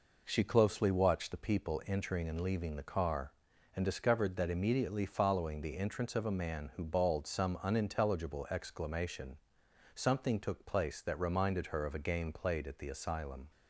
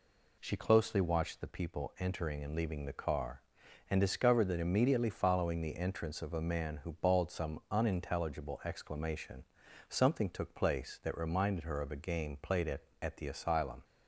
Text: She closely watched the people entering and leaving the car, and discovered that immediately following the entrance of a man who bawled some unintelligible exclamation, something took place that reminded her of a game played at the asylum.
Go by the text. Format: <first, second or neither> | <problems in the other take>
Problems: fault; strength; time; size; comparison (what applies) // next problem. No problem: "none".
first | says "at" twice; at 12.9 s